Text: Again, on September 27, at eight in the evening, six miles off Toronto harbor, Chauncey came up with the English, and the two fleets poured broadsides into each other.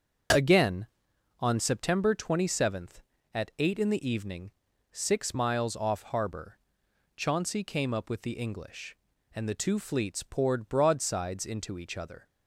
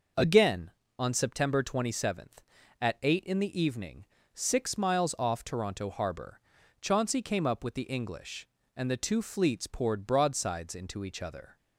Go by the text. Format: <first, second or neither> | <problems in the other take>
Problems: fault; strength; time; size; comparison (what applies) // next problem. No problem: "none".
second | starts louder than the rest; until 1.8 s; 6.5 dB // skips "Toronto"; at 6.0 s